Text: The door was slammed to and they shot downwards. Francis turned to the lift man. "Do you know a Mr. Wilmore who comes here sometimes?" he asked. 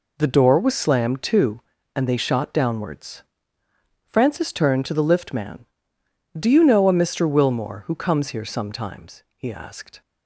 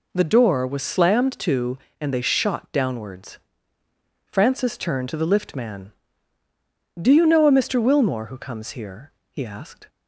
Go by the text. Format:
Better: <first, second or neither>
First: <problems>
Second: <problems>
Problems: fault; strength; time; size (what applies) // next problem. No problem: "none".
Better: first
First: none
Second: skips "sometimes"; at 9.1 s